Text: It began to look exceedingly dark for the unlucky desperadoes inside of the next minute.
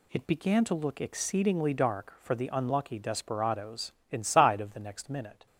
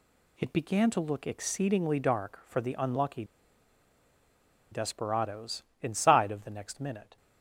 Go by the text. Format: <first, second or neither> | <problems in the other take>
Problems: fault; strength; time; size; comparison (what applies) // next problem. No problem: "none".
first | pauses between "unlucky" and "desperadoes"; strong; at 3.2 s; 1.4 s long // pauses between "desperadoes" and "inside"; slight; at 5.6 s; 0.16 s long; slight in the first